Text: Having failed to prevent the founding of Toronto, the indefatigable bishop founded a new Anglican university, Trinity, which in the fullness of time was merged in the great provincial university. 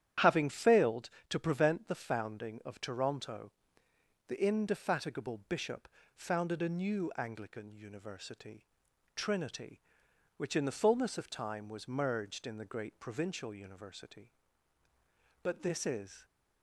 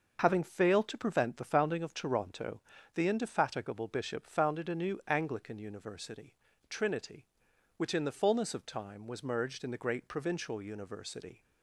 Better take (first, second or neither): second